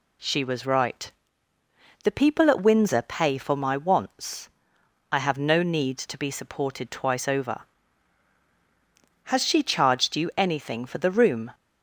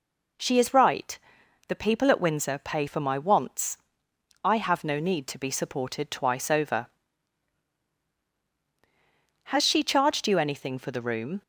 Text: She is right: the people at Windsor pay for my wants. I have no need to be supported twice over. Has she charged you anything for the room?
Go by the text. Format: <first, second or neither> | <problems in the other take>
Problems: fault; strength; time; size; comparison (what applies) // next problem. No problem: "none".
second | says "was" for "is"; at 0.4 s